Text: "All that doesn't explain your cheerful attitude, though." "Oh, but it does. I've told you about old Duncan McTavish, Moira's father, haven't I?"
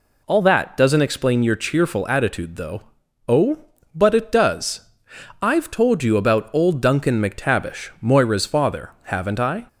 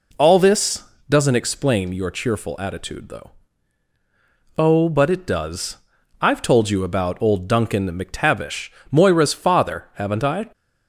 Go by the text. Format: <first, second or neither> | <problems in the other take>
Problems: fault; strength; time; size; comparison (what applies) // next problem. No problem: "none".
first | says "this" for "that"; at 0.3 s